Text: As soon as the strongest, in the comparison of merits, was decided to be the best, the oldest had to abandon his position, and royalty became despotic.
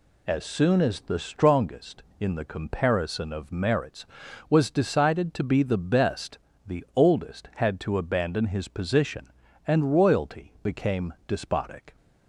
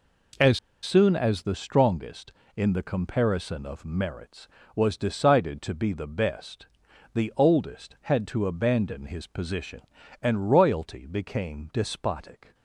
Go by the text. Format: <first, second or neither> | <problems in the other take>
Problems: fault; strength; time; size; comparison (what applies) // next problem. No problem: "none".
first | pauses between "As" and "soon"; slight; at 0.5 s; 0.24 s long